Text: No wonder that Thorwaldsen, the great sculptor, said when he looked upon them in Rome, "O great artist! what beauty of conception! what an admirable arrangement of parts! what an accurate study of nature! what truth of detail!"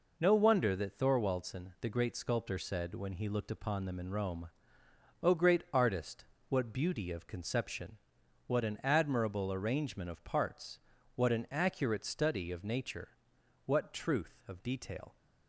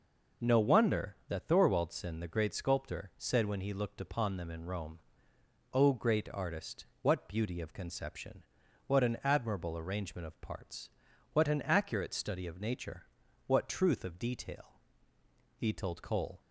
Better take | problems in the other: first | goes on to say "He told Cole"; noticeable; from 15.5 s on; 0.84 s long

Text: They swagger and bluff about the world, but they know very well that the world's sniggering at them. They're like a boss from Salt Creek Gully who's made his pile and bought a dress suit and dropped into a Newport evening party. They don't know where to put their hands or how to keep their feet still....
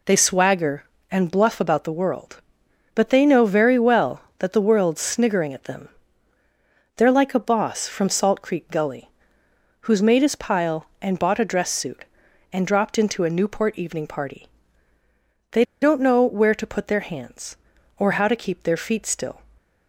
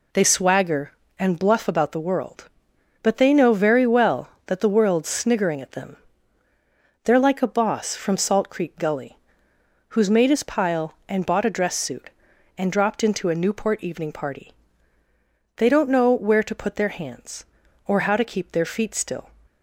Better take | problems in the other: second | pauses between "Gully" and "who's"; noticeable; at 9.0 s; 0.78 s long; noticeable in the second // pauses between "They" and "don't"; slight; at 15.6 s; 0.17 s long

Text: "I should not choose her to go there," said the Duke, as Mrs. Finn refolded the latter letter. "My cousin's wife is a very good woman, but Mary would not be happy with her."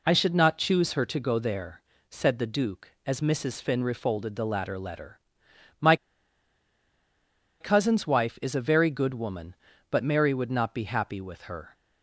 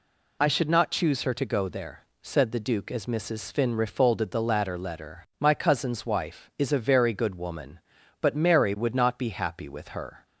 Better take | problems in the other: second | pauses between "My" and "cousin's"; strong; at 5.9 s; 1.6 s long

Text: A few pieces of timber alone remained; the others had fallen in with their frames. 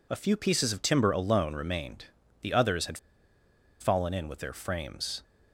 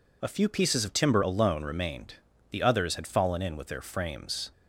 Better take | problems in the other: second | pauses between "had" and "fallen"; noticeable; at 2.9 s; 0.82 s long

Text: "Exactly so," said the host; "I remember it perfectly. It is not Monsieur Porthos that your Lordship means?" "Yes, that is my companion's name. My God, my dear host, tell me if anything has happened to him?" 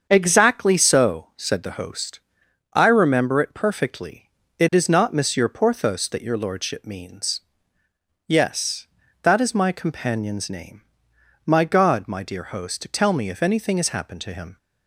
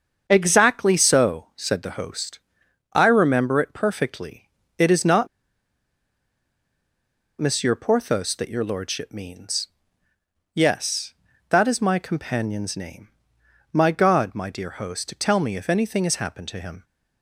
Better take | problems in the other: first | starts louder than the rest; until 1.2 s; 7 dB; also in the first // pauses between "not" and "Monsieur"; strong; at 5.2 s; 2.1 s long

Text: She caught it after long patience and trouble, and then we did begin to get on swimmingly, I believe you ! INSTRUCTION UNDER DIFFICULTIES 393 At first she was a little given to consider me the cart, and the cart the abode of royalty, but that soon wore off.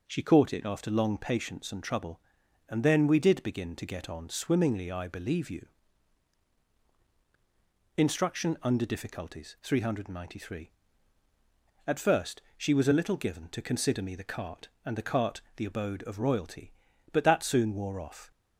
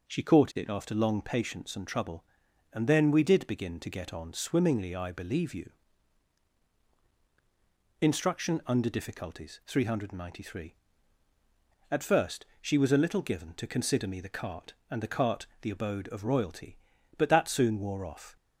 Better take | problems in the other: neither | pauses between "first" and "she"; slight; the same in both // pauses between "cart" and "the"; slight; the same in both

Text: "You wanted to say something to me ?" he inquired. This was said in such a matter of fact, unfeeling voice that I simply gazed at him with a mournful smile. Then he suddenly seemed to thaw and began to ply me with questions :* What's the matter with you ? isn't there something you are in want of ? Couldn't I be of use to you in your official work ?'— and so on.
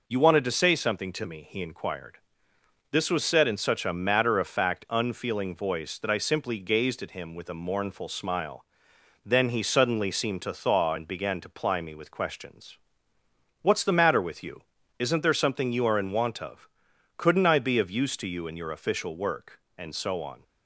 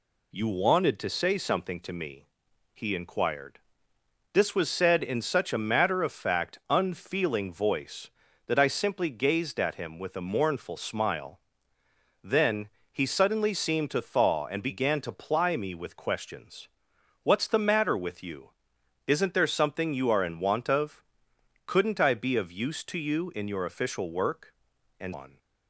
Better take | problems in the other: first | pauses between "Then" and "he"; slight; at 12.6 s; 0.24 s long // skips "so"; at 25.1 s

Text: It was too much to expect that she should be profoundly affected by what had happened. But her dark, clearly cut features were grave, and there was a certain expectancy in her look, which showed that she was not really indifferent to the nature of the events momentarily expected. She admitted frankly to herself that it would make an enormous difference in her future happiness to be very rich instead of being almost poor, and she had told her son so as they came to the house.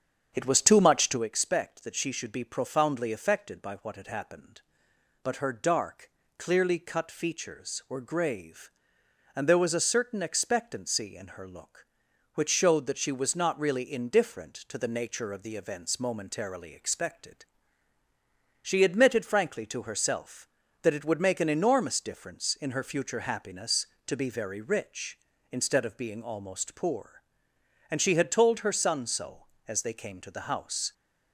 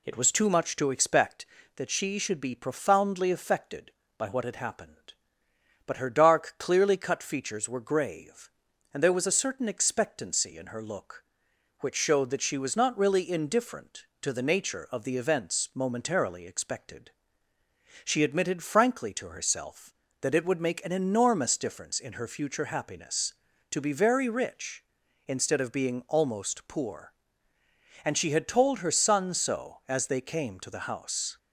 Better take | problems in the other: second | starts louder than the rest; strong; until 1.3 s; 8 dB

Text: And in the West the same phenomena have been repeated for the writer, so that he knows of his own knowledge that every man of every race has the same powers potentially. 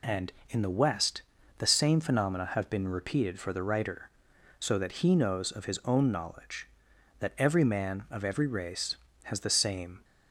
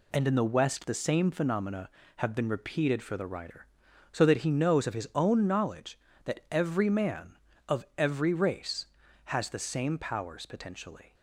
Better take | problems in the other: second | pauses between "West" and "the"; slight; at 1.2 s; 0.36 s long // stops before "powers potentially"; at 10.0 s

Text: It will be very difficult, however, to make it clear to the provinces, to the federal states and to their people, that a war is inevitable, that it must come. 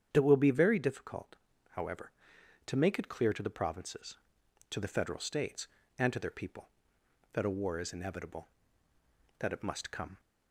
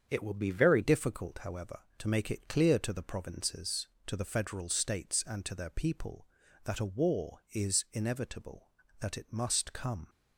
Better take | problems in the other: first | starts louder than the rest; strong; until 1.1 s; 7.5 dB; strong in the first // changes voice at "difficult"; from 0.8 s on; 9.2 s long

